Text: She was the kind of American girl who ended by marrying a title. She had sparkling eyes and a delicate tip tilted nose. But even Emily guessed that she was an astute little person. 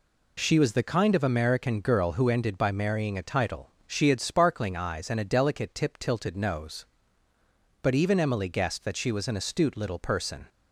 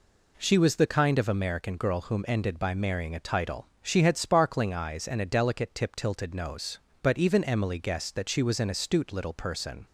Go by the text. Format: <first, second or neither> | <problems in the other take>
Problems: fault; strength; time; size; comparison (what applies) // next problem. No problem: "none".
first | says "whom" for "who"; at 2.0 s